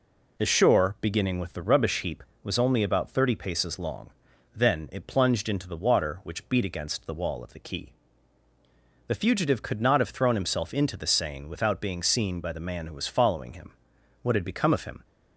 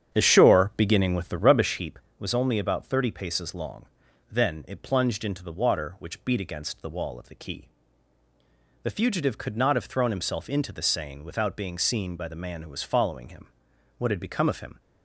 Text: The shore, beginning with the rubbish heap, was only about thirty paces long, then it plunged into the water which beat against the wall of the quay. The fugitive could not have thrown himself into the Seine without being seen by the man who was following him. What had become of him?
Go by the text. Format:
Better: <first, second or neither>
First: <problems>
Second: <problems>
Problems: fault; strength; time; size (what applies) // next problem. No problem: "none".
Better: first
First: none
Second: starts louder than the rest; strong; until 1.8 s; 8.5 dB